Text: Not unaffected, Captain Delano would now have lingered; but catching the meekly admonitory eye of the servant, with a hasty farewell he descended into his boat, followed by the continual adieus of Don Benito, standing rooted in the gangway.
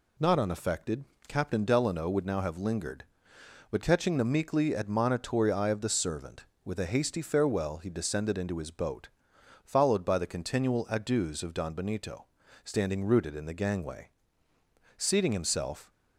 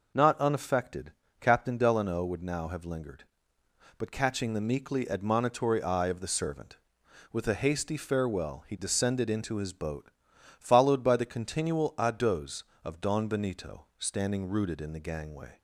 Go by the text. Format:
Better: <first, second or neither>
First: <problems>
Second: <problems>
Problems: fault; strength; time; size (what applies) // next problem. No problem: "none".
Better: second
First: goes on to say "Seating himself"; noticeable; from 14.9 s on; 0.94 s long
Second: none